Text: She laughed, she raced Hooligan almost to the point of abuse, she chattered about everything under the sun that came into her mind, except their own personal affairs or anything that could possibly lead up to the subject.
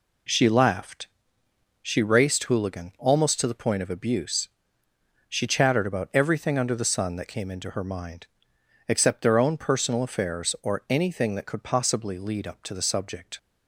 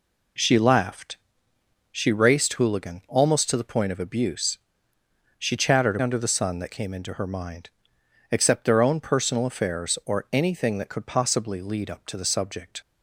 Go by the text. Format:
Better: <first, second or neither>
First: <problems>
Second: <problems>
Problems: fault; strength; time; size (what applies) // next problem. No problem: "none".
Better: first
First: none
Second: skips "about everything"; at 5.9 s